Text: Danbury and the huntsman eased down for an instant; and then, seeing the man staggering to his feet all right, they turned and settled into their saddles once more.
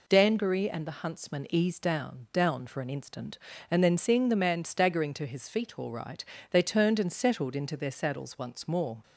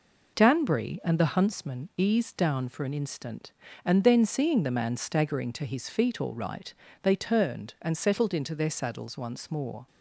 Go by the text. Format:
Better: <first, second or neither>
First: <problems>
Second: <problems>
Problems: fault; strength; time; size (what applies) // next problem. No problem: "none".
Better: second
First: says "down" twice; at 2.3 s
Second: none